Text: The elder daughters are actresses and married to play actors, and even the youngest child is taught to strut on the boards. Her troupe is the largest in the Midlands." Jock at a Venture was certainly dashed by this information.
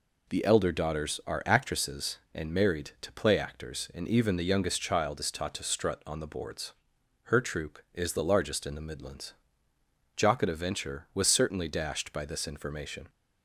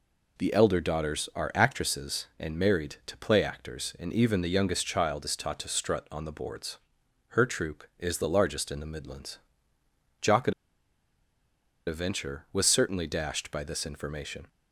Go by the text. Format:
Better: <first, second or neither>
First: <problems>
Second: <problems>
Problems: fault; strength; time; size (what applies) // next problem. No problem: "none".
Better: first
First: none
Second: pauses between "at" and "a"; strong; at 10.5 s; 1.3 s long